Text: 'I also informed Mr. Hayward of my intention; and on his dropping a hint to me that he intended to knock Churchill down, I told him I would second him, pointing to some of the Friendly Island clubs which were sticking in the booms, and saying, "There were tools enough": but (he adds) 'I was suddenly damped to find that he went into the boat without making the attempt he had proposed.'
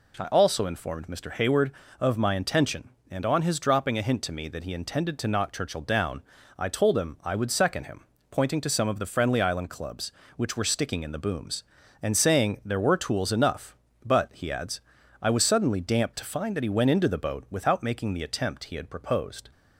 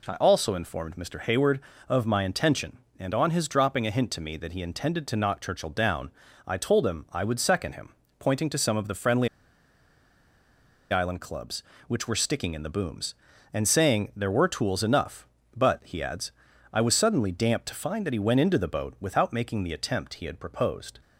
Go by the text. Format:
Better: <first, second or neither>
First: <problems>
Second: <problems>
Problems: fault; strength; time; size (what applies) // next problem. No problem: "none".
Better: first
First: none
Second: pauses between "Friendly" and "Island"; strong; at 9.2 s; 1.6 s long